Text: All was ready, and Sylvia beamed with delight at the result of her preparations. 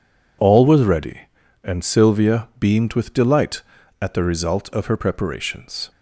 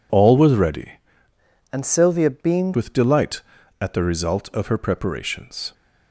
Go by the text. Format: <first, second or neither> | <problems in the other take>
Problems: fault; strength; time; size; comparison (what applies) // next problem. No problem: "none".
first | changes voice from "and" to "beamed"; from 1.7 to 2.7 s; 1.0 s long